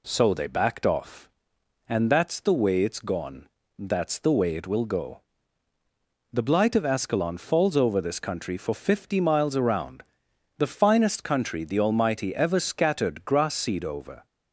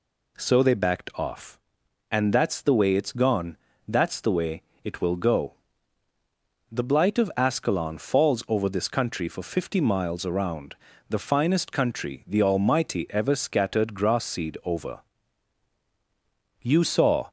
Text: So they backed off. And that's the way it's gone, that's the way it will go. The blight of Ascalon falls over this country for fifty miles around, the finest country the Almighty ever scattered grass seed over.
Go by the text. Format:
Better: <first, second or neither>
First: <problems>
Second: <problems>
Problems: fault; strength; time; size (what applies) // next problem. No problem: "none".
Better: first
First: none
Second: pauses between "way" and "it"; slight; at 4.6 s; 0.22 s long // goes on to say "You saw"; noticeable; from 16.5 s on; 0.70 s long